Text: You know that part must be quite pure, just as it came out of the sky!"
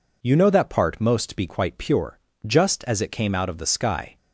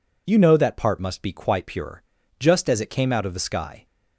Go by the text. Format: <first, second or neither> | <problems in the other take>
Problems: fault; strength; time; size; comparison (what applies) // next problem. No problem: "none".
second | says "most" for "must"; at 1.0 s